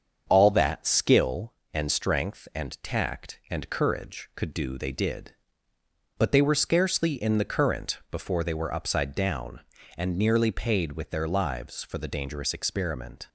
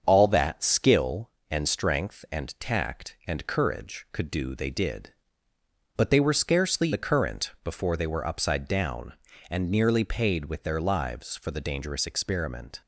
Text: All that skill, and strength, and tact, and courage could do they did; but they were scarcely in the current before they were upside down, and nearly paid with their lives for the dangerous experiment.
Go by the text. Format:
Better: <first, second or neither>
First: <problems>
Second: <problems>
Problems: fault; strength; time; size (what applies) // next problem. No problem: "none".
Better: first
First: starts louder than the rest; until 1.3 s; 7 dB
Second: starts louder than the rest; strong; until 1.0 s; 7 dB // skips "in"; at 6.9 s